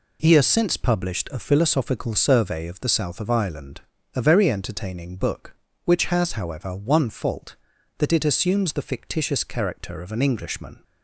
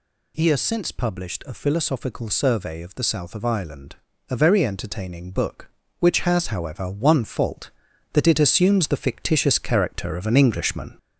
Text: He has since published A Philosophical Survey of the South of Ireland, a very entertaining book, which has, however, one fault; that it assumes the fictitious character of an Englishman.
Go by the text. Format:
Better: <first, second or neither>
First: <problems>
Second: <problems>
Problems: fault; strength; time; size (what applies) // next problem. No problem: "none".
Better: first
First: none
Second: gets louder; slight; throughout; 3.5 dB